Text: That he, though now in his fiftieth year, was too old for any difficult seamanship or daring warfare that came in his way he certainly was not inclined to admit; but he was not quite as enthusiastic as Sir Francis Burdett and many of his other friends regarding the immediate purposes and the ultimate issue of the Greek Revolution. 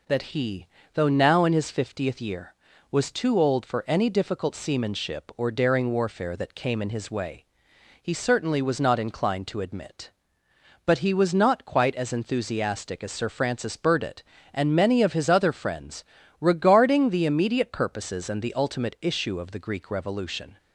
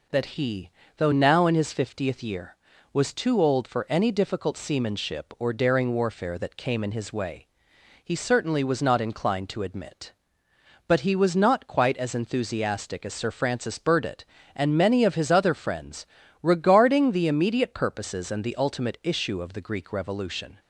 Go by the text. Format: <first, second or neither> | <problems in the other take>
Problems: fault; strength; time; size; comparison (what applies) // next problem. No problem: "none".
neither | pauses between "way" and "he"; noticeable; the same in both // pauses between "friends" and "regarding"; slight; the same in both